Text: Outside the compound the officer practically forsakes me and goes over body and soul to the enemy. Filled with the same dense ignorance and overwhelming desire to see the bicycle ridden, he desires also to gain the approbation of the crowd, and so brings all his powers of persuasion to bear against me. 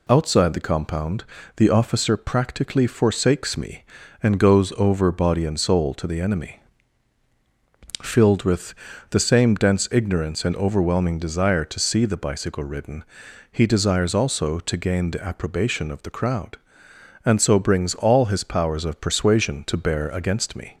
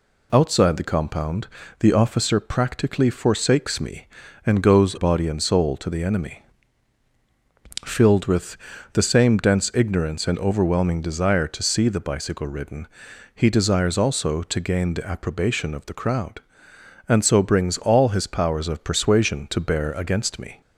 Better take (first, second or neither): first